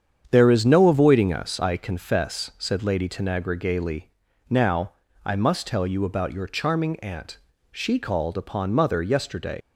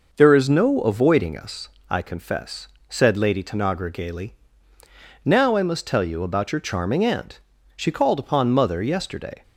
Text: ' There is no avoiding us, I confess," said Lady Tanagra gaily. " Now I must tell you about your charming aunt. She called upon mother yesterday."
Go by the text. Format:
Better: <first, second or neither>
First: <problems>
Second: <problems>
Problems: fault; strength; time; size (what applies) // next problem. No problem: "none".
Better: second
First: starts louder than the rest; strong; until 1.2 s; 8 dB // pauses between "Now" and "I"; slight; at 4.9 s; 0.30 s long // leaves "yesterday" unfinished; at 9.6 s; 110 ms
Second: none